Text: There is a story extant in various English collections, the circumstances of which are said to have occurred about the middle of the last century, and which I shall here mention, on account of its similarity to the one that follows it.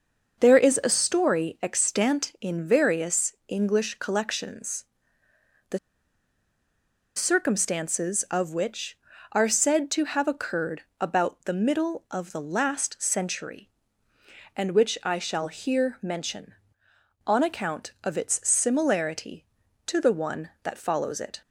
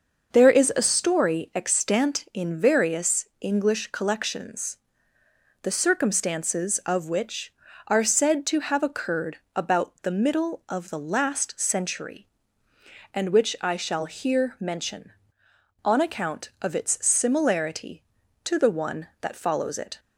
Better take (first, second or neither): second